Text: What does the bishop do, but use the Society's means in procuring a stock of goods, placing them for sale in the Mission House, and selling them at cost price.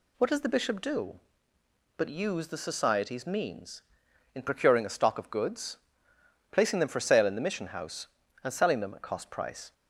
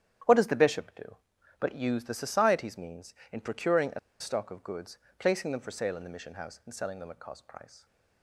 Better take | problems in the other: first | starts louder than the rest; strong; until 1.6 s; 10 dB // pauses between "a" and "stock"; slight; at 3.9 s; 0.21 s long

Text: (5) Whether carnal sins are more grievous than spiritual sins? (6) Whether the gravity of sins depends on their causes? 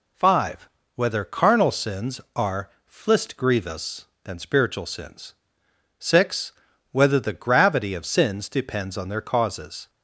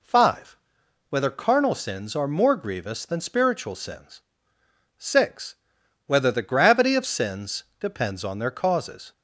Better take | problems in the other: second | says "flist" for "more"; at 2.8 s

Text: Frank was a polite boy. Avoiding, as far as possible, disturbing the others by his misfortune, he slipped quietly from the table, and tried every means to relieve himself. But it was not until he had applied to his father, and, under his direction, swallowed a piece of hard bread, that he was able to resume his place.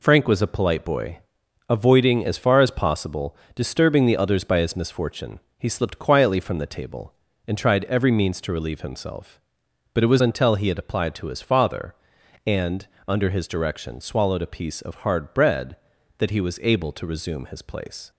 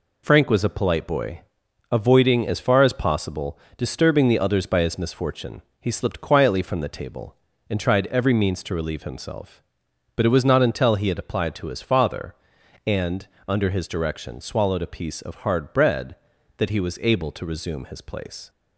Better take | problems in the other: second | skips "not"; at 10.2 s

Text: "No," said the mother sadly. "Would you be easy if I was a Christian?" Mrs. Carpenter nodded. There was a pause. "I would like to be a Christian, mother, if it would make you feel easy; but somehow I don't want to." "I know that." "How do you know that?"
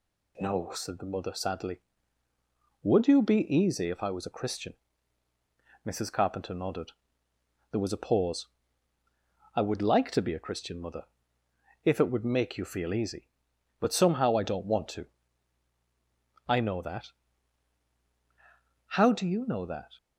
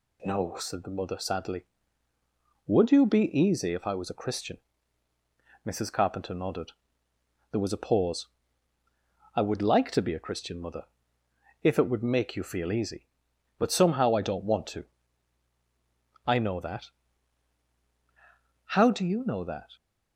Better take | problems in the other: neither | none

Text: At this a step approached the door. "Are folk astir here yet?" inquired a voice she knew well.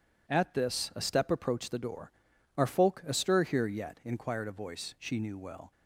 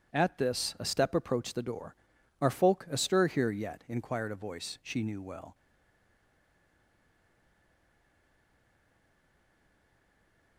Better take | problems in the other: first | stays silent after the last word; strong; from 5.5 s on; 5.0 s long

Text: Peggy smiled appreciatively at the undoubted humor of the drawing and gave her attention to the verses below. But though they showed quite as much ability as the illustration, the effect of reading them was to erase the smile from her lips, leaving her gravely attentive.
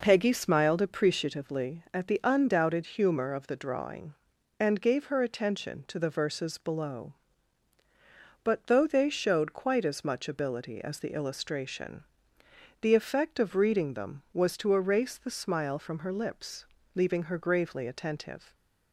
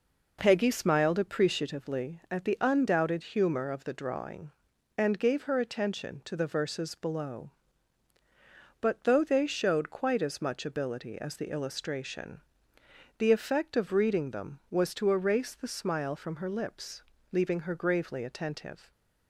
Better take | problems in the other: neither | none

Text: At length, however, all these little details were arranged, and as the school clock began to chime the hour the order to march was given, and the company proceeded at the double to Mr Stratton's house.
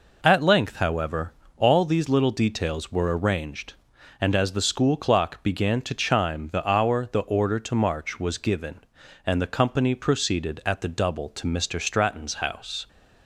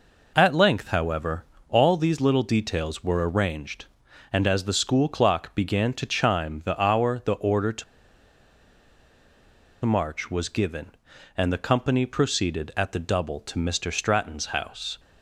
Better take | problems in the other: first | pauses between "to" and "march"; strong; at 7.8 s; 2.0 s long

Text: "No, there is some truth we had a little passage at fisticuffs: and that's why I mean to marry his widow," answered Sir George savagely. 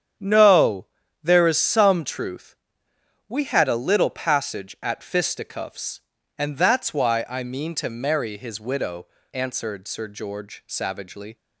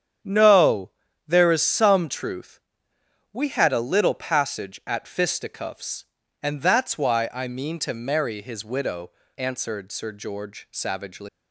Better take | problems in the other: first | starts louder than the rest; strong; until 1.6 s; 8.5 dB; strong in the first // pauses between "truth" and "we"; noticeable; at 2.5 s; 0.72 s long; noticeable in the first // leaves "savagely" unfinished; at 11.2 s; 110 ms

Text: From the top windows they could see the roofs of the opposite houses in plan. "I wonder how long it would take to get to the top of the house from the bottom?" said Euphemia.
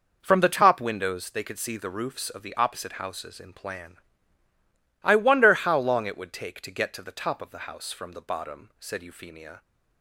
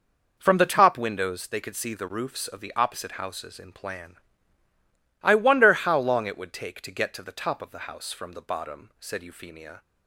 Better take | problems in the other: neither | none

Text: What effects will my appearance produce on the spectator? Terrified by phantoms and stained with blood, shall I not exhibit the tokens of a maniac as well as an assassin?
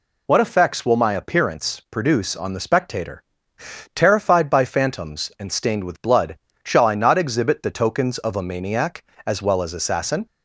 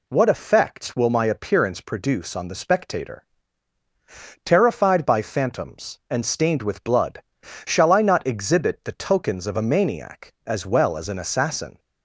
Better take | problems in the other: second | skips "an"; at 9.7 s

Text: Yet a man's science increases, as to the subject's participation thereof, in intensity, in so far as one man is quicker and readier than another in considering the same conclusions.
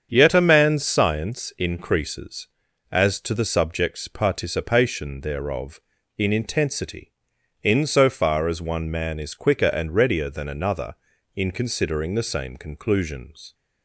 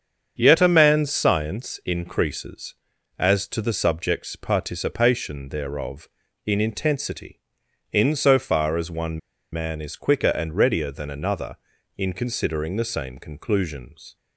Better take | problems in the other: first | starts louder than the rest; strong; until 1.3 s; 7.5 dB; strong in the first // pauses between "one" and "man"; slight; at 9.1 s; 0.33 s long

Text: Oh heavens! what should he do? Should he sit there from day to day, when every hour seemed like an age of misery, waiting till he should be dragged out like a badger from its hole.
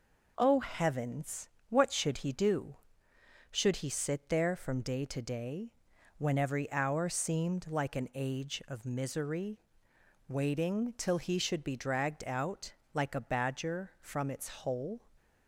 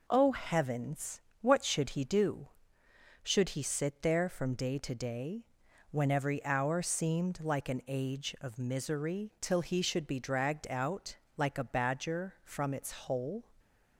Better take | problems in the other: first | skips "waiting"; at 9.3 s // pauses between "out" and "like"; slight; at 11.1 s; 0.22 s long; slight in the first

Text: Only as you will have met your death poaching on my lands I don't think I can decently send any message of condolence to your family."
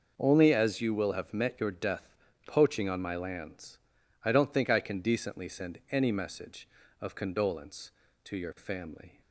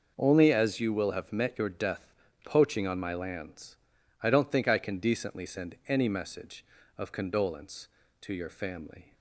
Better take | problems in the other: neither | pauses between "death" and "poaching"; the same in both // pauses between "lands" and "I"; the same in both

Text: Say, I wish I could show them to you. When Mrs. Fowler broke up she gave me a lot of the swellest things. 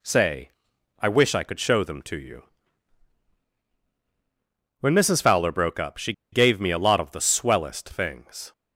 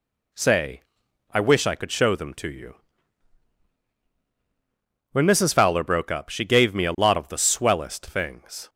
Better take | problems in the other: second | pauses between "she" and "gave"; slight; at 6.1 s; 0.20 s long

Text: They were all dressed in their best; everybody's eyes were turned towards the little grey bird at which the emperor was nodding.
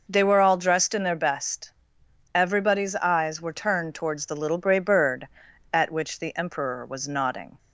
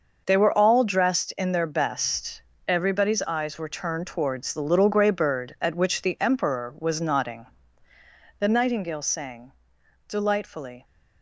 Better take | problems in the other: first | starts louder than the rest; noticeable; until 1.2 s; 6 dB // goes on to say "The nightingale sang delightfully"; strong; from 8.3 s on; 2.4 s long

